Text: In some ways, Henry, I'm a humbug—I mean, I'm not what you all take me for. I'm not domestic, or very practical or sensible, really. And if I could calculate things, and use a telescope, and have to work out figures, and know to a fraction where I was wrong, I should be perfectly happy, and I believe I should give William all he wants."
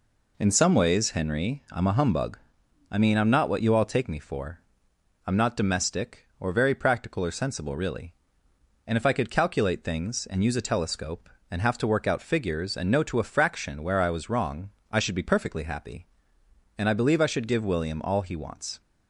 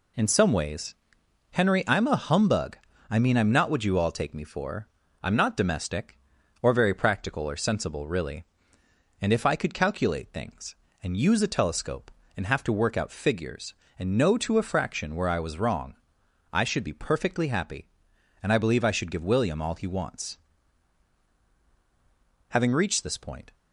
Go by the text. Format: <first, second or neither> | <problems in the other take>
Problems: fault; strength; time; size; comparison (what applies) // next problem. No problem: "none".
first | goes on to say "Having reached this point"; noticeable; from 22.4 s on; 1.0 s long